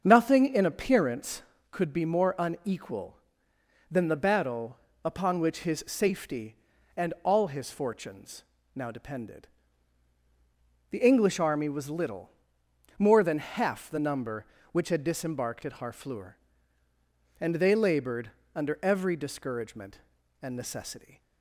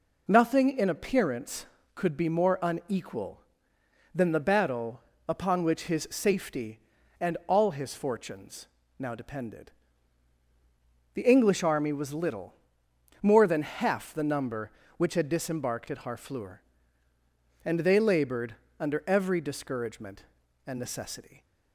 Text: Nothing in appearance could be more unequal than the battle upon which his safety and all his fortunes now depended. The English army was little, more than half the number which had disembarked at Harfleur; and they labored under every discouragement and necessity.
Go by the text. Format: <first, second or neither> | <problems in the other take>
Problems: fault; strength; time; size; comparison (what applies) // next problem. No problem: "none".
second | starts louder than the rest; until 1.5 s; 7 dB // pauses between "battle" and "upon"; slight; at 4.7 s; 0.28 s long; slight in the second // pauses between "fortunes" and "now"; slight; at 8.4 s; 0.32 s long; slight in the second // pauses between "labored" and "under"; slight; at 18.3 s; 0.24 s long; slight in the second